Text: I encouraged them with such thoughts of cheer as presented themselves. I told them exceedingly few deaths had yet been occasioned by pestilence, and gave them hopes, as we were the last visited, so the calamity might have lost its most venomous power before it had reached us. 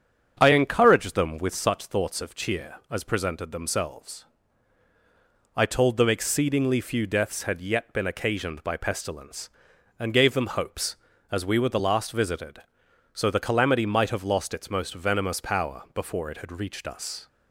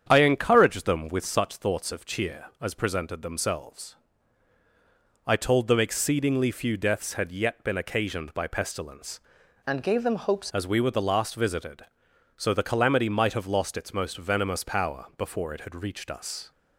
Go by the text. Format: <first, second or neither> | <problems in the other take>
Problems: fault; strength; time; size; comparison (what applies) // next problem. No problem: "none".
first | starts louder than the rest; strong; until 1.1 s; 8.5 dB; strong in the first // changes voice from "and" to "hopes"; from 9.6 to 10.5 s; 0.9 s long